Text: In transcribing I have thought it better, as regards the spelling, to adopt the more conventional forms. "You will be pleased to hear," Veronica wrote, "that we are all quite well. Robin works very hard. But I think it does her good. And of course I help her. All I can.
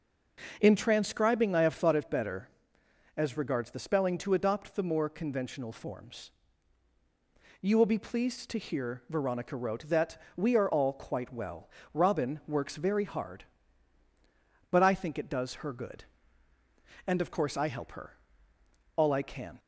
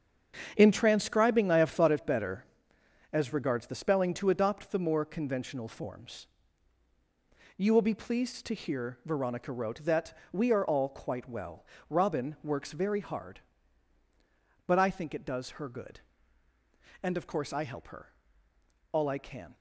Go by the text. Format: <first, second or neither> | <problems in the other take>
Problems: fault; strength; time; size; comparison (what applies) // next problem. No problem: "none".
first | gets quieter; strong; throughout; 9.5 dB // pauses between "that" and "we"; slight; at 10.1 s; 0.16 s long; slight in the first